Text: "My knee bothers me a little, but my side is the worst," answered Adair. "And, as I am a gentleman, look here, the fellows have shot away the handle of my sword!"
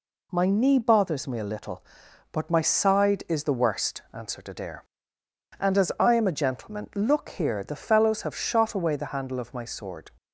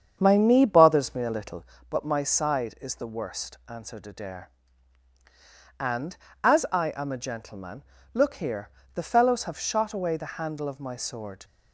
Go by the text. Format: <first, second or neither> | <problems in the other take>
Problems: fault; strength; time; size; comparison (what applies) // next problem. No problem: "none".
first | starts louder than the rest; strong; until 1.7 s; 7.5 dB